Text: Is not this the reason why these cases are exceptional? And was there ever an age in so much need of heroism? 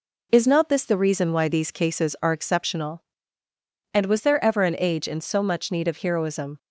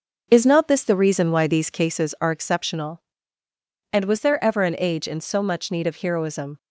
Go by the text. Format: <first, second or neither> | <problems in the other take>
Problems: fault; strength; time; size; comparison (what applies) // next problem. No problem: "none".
first | starts louder than the rest; until 2.0 s; 6.5 dB